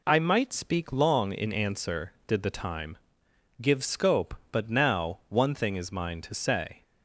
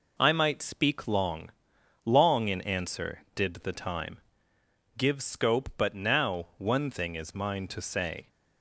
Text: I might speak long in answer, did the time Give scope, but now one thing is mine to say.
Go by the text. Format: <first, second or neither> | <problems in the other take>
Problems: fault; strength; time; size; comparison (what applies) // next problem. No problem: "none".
first | says "long" twice; at 2.0 s // pauses between "time" and "Give"; noticeable; at 4.1 s; 0.78 s long; noticeable in the first